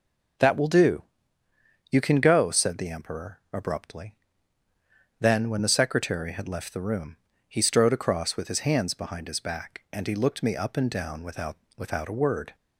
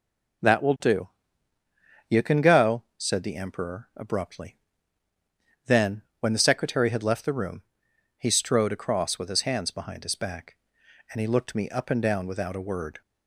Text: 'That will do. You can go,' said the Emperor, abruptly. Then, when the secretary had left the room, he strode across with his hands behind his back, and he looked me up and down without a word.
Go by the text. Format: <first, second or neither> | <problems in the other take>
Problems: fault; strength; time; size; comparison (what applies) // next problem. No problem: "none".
second | says "without" twice; at 11.7 s